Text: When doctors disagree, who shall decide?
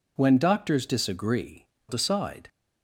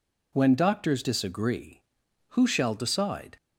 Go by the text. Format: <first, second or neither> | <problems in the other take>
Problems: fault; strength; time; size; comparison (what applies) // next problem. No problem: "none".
second | skips "who shall"; at 1.7 s